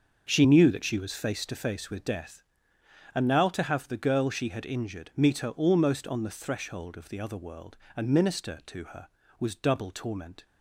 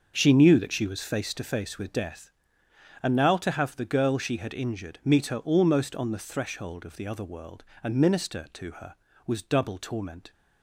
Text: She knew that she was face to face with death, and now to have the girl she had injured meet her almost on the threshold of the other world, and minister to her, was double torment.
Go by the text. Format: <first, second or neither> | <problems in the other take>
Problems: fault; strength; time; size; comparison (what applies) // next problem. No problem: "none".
neither | starts louder than the rest; the same in both